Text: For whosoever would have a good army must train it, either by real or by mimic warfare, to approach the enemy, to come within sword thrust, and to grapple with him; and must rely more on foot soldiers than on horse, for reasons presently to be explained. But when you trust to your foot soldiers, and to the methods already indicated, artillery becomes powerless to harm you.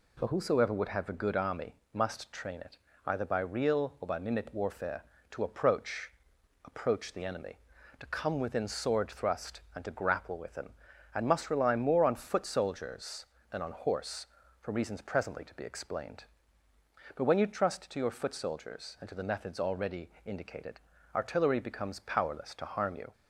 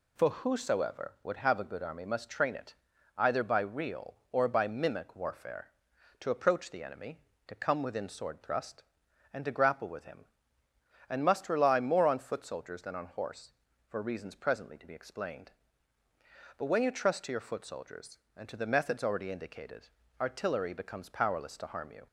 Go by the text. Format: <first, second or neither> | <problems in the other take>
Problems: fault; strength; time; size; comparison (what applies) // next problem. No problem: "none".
second | pauses between "army" and "must"; slight; at 1.7 s; 0.18 s long // says "approach" twice; at 6.6 s // pauses between "already" and "indicated"; slight; at 20.1 s; 0.16 s long